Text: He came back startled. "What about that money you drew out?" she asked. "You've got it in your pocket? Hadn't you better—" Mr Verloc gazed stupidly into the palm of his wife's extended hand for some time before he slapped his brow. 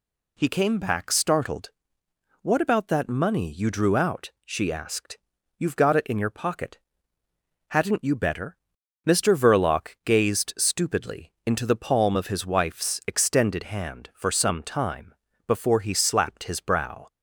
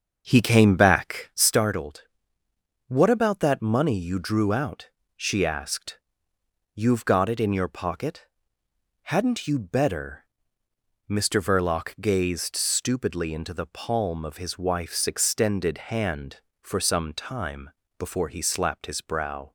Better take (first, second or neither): first